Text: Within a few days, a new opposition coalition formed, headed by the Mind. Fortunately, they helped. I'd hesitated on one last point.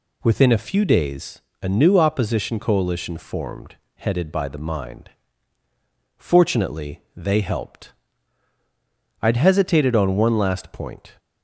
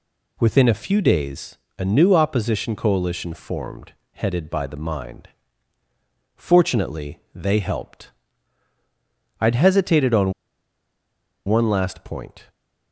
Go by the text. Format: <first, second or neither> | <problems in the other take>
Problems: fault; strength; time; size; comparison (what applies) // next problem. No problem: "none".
first | pauses between "on" and "one"; at 10.3 s; 1.1 s long